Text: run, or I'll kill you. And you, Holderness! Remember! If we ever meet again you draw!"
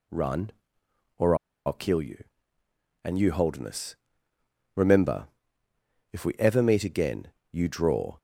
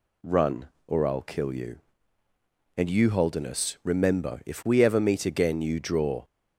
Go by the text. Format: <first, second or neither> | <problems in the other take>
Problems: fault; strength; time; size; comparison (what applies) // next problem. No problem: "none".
second | pauses between "or" and "I'll"; slight; at 1.3 s; 0.30 s long // pauses between "again" and "you"; slight; at 7.2 s; 0.24 s long